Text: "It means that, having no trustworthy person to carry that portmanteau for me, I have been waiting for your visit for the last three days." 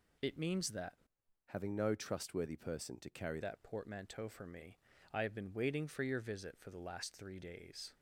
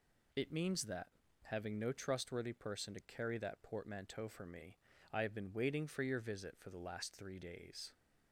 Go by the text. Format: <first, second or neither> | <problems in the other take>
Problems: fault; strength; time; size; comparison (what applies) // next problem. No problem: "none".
second | changes voice from "having" to "carry"; from 1.4 to 3.4 s; 2.0 s long